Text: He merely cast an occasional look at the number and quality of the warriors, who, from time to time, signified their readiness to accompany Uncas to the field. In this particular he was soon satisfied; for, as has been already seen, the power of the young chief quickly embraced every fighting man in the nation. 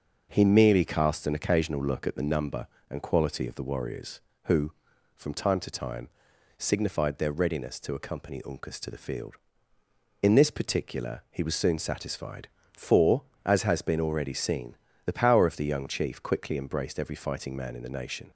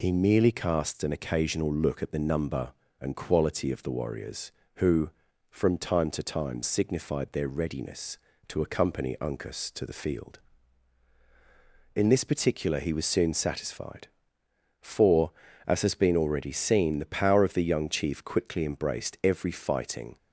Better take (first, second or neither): first